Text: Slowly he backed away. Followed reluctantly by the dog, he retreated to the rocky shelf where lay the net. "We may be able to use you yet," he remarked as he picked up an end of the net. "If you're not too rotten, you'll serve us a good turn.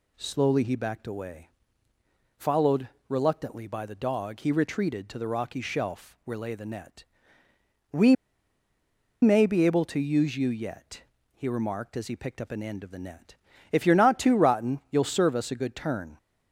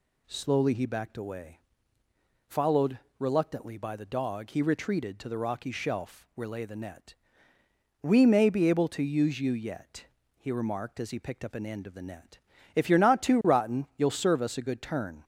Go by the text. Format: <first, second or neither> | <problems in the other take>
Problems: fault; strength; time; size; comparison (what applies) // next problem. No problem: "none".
second | pauses between "Followed" and "reluctantly"; slight; at 2.8 s; 0.20 s long; slight in the second // pauses between "We" and "may"; at 8.1 s; 1.0 s long